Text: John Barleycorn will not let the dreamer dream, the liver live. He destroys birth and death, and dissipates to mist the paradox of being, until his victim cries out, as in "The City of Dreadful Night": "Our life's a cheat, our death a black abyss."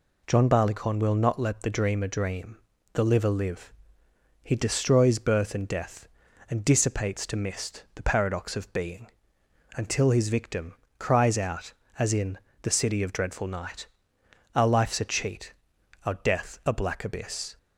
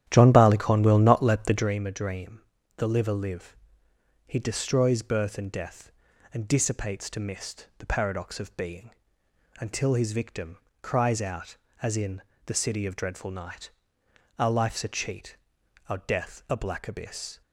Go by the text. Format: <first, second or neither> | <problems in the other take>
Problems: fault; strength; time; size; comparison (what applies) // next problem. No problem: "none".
first | starts louder than the rest; strong; until 1.7 s; 11 dB // pauses between "victim" and "cries"; slight; at 10.5 s; 0.24 s long; slight in the first // pauses between "in" and "The"; slight; at 12.2 s; 0.24 s long; slight in the first